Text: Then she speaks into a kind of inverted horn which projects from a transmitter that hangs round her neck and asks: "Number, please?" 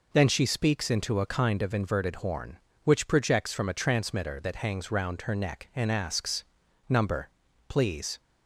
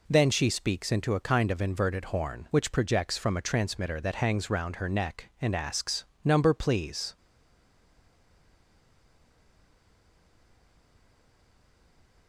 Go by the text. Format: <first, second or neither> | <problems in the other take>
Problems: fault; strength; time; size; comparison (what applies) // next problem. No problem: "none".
first | stays silent after the last word; strong; from 7.1 s on; 5.1 s long